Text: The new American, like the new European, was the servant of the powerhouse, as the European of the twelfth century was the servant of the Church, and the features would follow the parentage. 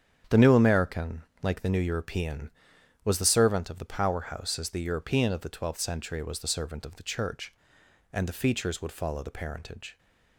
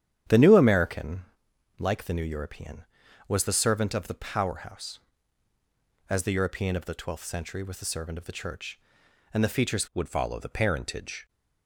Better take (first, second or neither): first